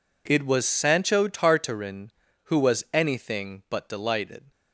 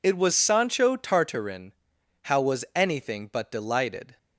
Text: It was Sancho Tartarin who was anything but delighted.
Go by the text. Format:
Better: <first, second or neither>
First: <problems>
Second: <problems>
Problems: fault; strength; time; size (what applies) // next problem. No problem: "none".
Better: first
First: none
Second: says "how" for "who"; at 2.2 s